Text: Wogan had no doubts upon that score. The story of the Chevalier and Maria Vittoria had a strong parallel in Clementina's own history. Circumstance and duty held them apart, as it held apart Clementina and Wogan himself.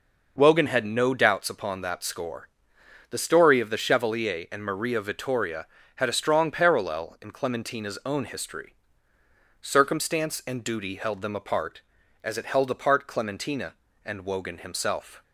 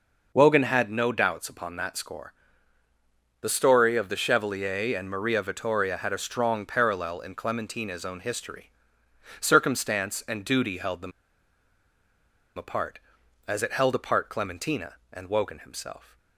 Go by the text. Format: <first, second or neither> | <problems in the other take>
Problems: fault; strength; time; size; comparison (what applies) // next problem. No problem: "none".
first | pauses between "them" and "apart"; strong; at 11.1 s; 1.4 s long